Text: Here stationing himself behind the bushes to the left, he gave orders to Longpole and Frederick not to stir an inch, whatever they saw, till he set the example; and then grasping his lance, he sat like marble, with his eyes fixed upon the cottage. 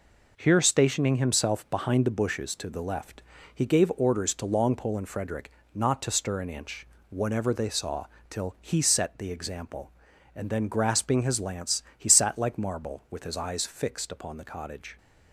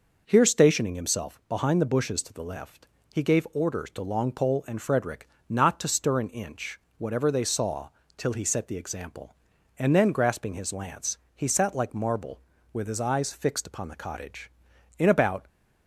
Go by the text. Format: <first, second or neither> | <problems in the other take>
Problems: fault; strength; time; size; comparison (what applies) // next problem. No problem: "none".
first | pauses between "Frederick" and "not"; slight; at 5.2 s; 0.22 s long; slight in the first // goes on to say "In about"; from 14.9 s on; 0.50 s long